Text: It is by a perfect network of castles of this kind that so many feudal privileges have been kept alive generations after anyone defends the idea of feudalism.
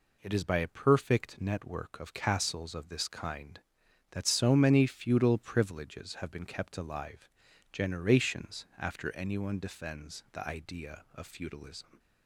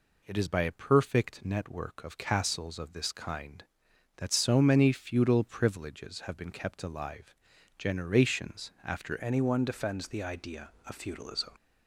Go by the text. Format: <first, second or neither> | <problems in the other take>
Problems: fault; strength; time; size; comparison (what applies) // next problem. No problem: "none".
first | pauses between "alive" and "generations"; at 7.3 s; 0.42 s long; also in the first // changes voice at "anyone"; from 9.1 s on; 2.4 s long